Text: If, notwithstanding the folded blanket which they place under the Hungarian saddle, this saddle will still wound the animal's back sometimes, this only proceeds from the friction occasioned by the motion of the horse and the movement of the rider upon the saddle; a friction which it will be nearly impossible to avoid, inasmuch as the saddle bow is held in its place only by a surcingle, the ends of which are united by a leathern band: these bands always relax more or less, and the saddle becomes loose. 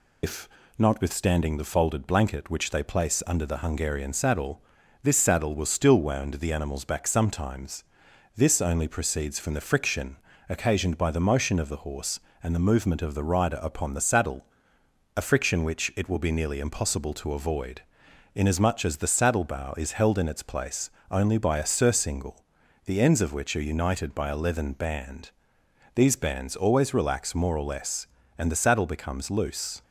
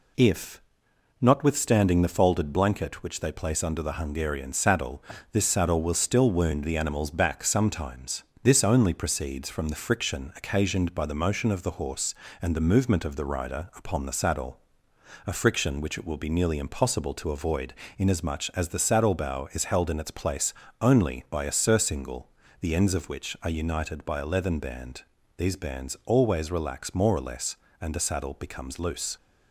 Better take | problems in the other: second | loses the start of "If"; at 0.2 s; 150 ms // pauses between "friction" and "occasioned"; slight; at 10.1 s; 0.32 s long // pauses between "place" and "only"; slight; at 20.8 s; 0.22 s long; slight in the second

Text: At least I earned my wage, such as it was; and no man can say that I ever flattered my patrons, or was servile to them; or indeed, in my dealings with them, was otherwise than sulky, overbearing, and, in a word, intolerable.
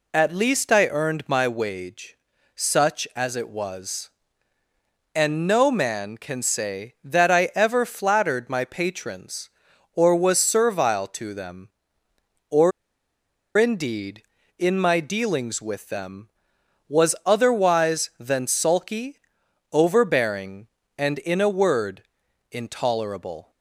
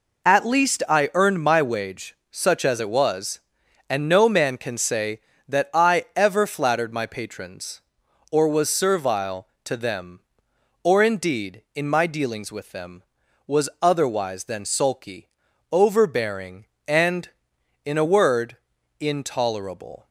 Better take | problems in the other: second | pauses between "or" and "indeed"; noticeable; at 12.7 s; 0.86 s long

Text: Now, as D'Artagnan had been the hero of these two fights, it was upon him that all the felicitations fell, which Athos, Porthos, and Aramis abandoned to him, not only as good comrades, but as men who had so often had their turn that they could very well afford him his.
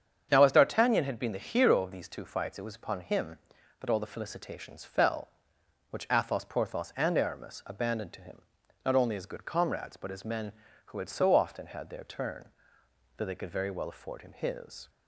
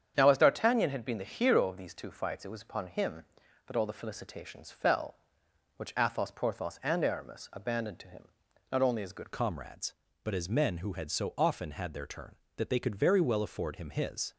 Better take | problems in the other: first | starts louder than the rest; strong; until 1.1 s; 8 dB; strong in the first // changes voice at "comrades"; from 9.3 s on; 5.0 s long

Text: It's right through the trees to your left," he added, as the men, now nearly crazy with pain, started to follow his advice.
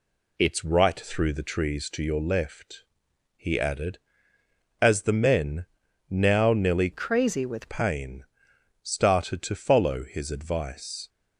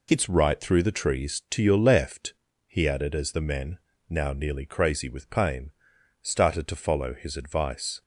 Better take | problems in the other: second | changes voice from "crazy" to "with"; from 6.9 to 7.6 s; 0.7 s long

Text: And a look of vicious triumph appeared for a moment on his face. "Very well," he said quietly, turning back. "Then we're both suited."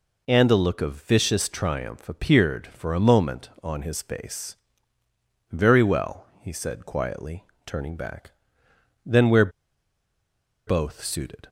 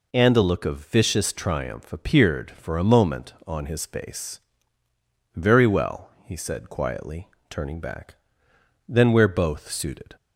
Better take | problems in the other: second | pauses between "we're" and "both"; at 9.4 s; 1.1 s long

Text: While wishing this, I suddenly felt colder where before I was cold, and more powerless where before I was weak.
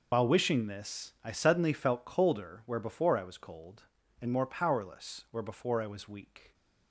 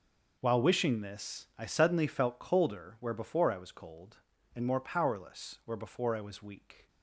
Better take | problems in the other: second | loses the start of "While"; at 0.1 s; 70 ms

